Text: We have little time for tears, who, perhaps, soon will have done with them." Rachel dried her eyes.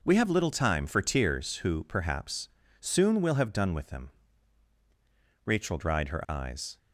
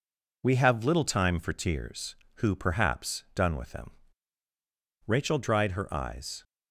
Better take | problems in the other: first | skips "soon will have"; at 3.2 s

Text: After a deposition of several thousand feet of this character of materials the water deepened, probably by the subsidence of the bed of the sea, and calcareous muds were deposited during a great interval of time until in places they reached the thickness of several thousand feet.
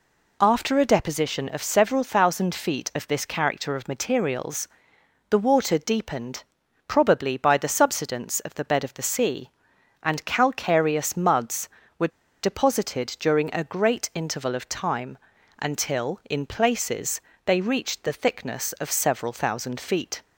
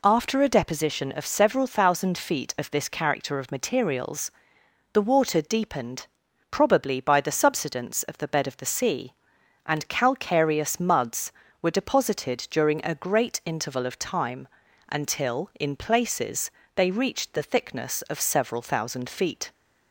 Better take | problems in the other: second | pauses between "materials" and "the"; noticeable; at 4.6 s; 0.62 s long; noticeable in the second // pauses between "were" and "deposited"; slight; at 12.1 s; 0.33 s long // pauses between "time" and "until"; at 15.1 s; 0.42 s long; also in the second // pauses between "places" and "they"; slight; at 17.2 s; 0.24 s long; slight in the second

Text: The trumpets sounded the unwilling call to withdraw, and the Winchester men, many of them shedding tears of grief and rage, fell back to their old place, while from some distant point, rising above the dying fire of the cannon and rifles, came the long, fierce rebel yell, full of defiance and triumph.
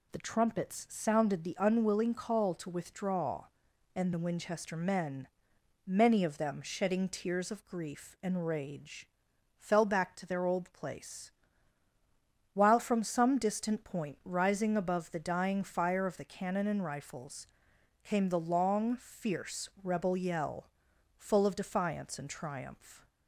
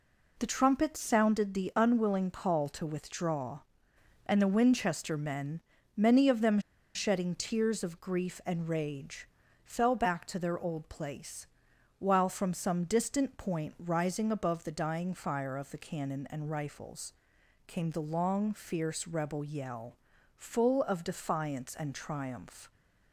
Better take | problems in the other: first | pauses between "them" and "shedding"; slight; at 6.5 s; 0.35 s long

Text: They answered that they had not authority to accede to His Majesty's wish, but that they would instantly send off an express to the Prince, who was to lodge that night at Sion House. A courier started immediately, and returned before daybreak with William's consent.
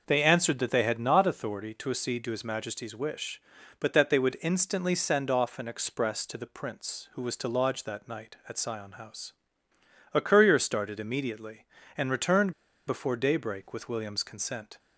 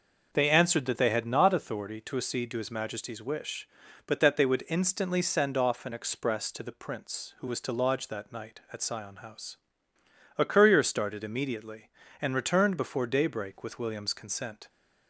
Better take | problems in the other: second | pauses between "returned" and "before"; slight; at 12.5 s; 0.34 s long

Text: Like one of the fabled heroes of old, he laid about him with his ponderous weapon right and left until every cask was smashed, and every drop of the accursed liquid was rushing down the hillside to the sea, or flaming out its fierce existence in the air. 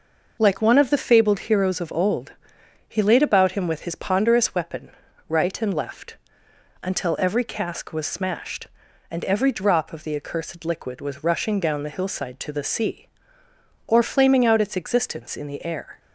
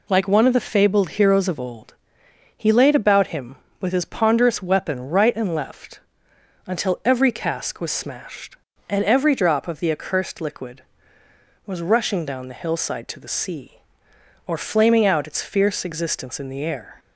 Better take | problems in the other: second | pauses between "weapon" and "right"; at 4.8 s; 0.38 s long // pauses between "left" and "until"; noticeable; at 6.1 s; 0.66 s long; noticeable in the second // skips "fierce"; at 14.7 s

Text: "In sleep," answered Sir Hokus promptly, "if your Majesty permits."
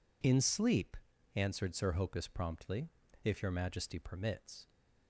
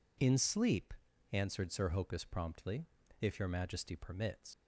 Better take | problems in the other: first | leaves "permits" unfinished; at 4.5 s; 115 ms

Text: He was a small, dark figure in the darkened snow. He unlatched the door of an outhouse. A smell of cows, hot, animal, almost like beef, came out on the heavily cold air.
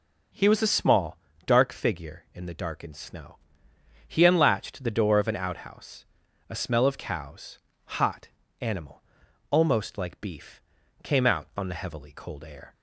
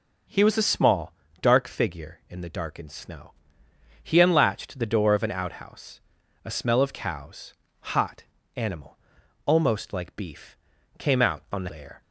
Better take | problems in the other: first | skips "heavily cold"; at 11.7 s

